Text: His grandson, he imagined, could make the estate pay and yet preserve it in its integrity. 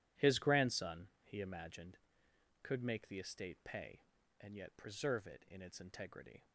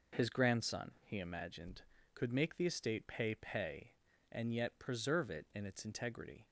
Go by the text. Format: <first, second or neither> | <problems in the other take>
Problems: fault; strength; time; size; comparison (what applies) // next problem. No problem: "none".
first | says "pay" twice; at 3.3 s